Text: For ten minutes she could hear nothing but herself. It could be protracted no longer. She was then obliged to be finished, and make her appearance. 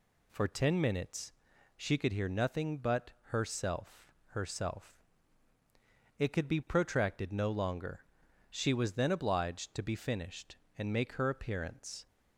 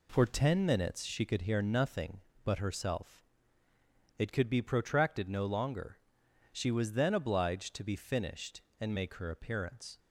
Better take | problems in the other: second | pauses between "minutes" and "she"; at 1.3 s; 0.44 s long // says "herself" twice; at 4.2 s

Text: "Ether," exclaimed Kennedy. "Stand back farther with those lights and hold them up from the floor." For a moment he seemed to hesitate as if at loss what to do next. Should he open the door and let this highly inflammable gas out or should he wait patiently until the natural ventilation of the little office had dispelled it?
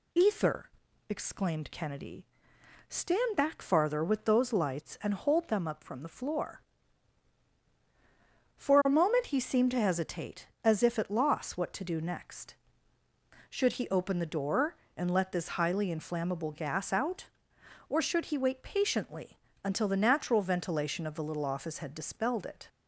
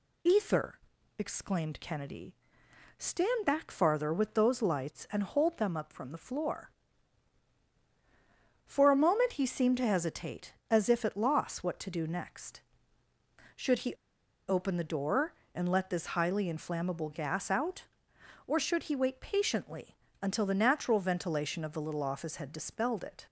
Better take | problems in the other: first | pauses between "he" and "open"; noticeable; at 13.9 s; 0.53 s long // pauses between "patiently" and "until"; slight; at 19.9 s; 0.28 s long; slight in the first

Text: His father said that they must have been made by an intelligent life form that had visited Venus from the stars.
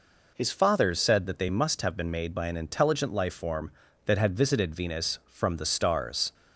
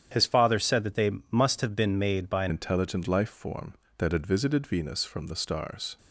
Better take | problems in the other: first | starts louder than the rest; strong; until 1.3 s; 9 dB // pauses between "they" and "must"; slight; at 1.1 s; 0.20 s long // changes voice at "intelligent"; from 2.4 s on; 3.5 s long

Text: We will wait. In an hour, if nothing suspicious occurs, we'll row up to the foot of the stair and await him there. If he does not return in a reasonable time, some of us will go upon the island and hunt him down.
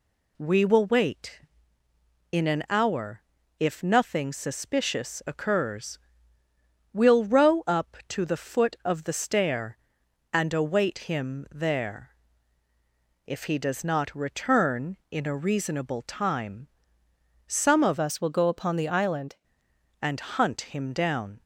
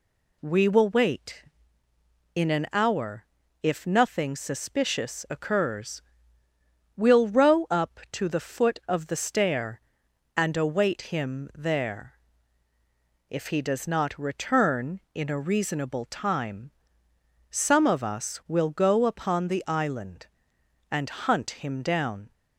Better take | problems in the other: second | changes voice from "us" to "island"; from 17.9 to 19.3 s; 1.4 s long

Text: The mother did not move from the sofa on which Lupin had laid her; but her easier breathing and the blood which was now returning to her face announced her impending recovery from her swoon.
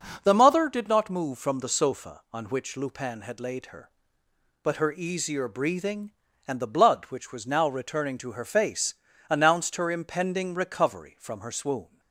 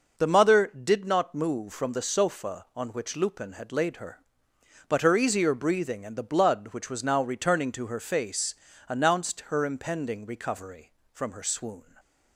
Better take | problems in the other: neither | pauses between "face" and "announced"; slight; the same in both

